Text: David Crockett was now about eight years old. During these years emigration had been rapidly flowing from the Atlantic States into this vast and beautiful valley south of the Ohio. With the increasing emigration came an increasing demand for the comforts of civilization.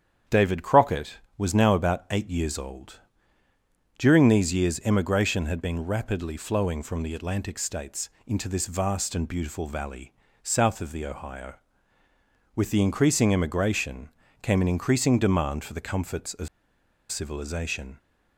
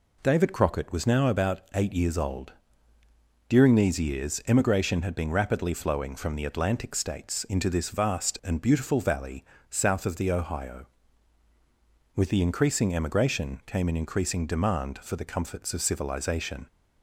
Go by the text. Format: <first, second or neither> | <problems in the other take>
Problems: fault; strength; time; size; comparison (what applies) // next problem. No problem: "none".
second | starts louder than the rest; strong; until 1.4 s; 8.5 dB // pauses between "States" and "into"; slight; at 8.0 s; 0.18 s long // pauses between "valley" and "south"; slight; at 10.1 s; 0.32 s long; slight in the second // pauses between "emigration" and "came"; slight; at 14.0 s; 0.34 s long // pauses between "of" and "civilization"; noticeable; at 16.4 s; 0.63 s long